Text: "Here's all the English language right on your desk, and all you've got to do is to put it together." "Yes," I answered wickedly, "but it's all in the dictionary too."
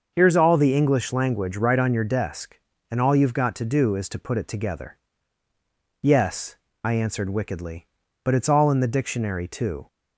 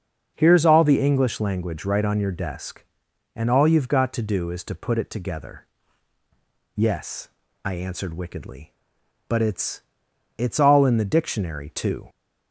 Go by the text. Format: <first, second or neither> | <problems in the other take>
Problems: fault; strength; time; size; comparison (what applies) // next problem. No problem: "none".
first | starts louder than the rest; until 1.3 s; 6.5 dB; also in the first // says "it's" twice; at 10.3 s